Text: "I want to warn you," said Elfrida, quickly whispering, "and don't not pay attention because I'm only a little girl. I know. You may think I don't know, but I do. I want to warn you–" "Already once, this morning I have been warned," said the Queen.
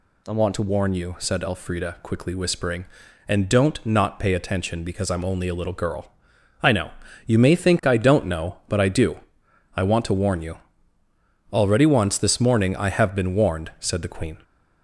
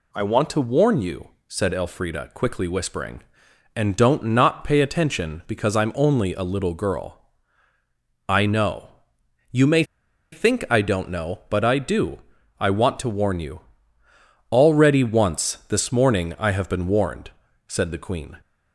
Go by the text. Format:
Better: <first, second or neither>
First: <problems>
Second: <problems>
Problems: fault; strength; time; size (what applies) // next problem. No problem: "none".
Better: first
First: none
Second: pauses between "may" and "think"; noticeable; at 9.8 s; 0.48 s long